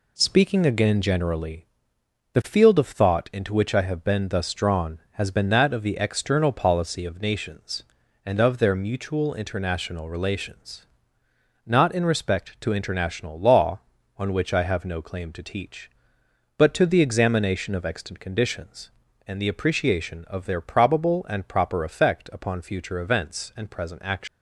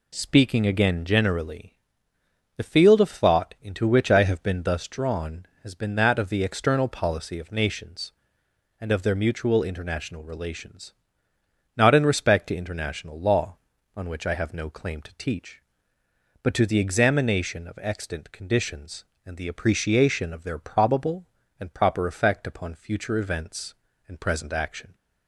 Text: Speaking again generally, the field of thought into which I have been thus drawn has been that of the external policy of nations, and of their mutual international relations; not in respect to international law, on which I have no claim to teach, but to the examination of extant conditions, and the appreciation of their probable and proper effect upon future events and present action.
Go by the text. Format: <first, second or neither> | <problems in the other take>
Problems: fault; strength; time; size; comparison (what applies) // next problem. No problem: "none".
second | leaves "action" unfinished; at 24.2 s; 105 ms